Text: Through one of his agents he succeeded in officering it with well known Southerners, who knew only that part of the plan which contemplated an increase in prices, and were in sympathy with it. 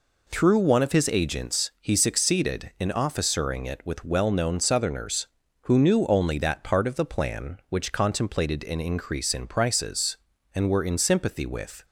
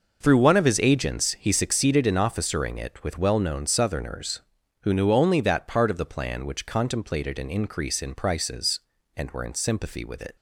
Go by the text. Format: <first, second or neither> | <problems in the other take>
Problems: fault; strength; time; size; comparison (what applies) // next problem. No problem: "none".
second | stops before "it"; at 11.8 s